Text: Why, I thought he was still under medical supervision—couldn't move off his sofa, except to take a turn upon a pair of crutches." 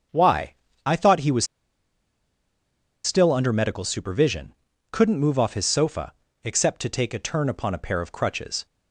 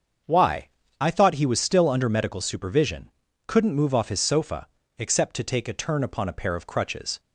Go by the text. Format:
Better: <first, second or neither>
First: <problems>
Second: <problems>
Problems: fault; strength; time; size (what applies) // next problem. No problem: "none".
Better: second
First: starts louder than the rest; until 1.4 s; 6.5 dB // pauses between "was" and "still"; strong; at 1.4 s; 1.5 s long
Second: starts louder than the rest; until 1.5 s; 6.5 dB